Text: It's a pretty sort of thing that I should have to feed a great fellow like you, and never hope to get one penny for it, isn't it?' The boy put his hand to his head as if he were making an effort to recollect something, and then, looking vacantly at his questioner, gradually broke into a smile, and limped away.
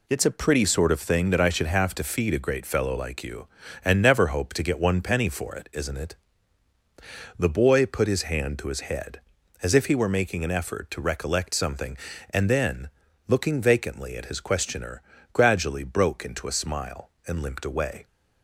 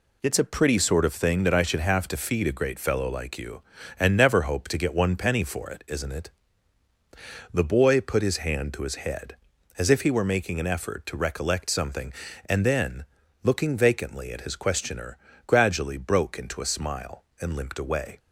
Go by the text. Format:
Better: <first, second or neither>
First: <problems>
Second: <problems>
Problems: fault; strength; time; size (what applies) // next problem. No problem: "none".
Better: neither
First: none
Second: none